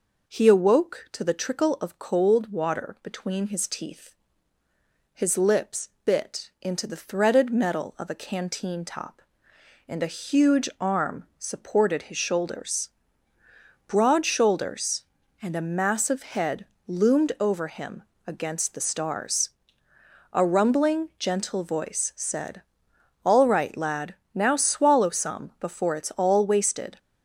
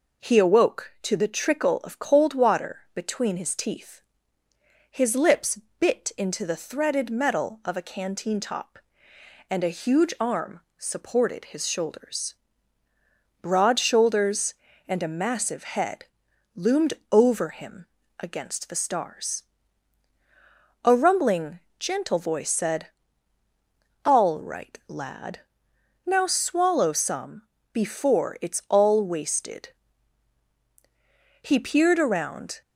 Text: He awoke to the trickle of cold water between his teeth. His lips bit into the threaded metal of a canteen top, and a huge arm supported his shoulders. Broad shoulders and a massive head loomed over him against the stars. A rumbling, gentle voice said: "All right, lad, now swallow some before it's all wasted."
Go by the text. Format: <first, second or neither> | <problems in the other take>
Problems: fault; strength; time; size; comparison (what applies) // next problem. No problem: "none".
first | pauses between "lips" and "bit"; slight; at 5.5 s; 0.20 s long // pauses between "arm" and "supported"; slight; at 10.6 s; 0.16 s long // pauses between "head" and "loomed"; noticeable; at 16.0 s; 0.50 s long; slight in the first // pauses between "loomed" and "over"; slight; at 16.9 s; 0.18 s long // pauses between "him" and "against"; slight; at 17.8 s; 0.32 s long; slight in the first // pauses between "some" and "before"; slight; at 27.4 s; 0.30 s long // goes on to say "He peered around"; noticeable; from 31.4 s on; 1.1 s long